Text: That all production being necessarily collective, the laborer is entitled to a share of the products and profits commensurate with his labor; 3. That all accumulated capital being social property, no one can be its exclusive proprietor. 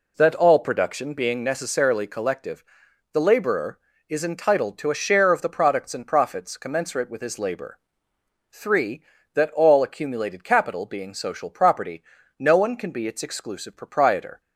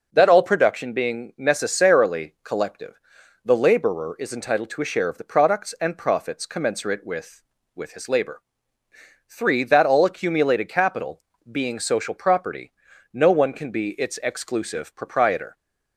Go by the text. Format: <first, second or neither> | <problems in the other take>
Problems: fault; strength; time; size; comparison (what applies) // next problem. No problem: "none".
first | says "with" twice; at 7.7 s // pauses between "capital" and "being"; slight; at 11.2 s; 0.28 s long